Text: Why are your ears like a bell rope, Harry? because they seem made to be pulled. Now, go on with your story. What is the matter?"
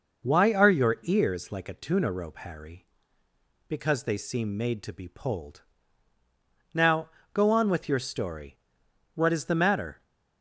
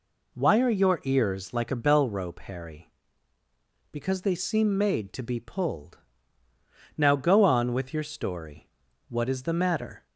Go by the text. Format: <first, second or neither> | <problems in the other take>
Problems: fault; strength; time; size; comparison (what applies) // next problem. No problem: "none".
second | says "tuna" for "bell"; at 1.7 s